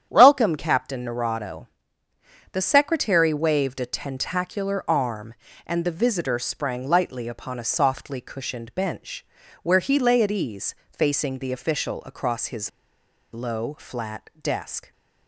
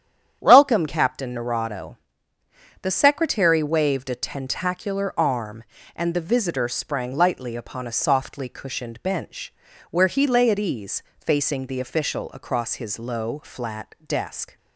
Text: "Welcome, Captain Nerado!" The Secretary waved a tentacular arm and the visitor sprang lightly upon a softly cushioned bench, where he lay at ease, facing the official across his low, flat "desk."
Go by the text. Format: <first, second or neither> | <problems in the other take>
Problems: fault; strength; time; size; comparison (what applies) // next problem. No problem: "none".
second | starts louder than the rest; strong; until 1.1 s; 9.5 dB; strong in the second // pauses between "his" and "low"; noticeable; at 12.6 s; 0.63 s long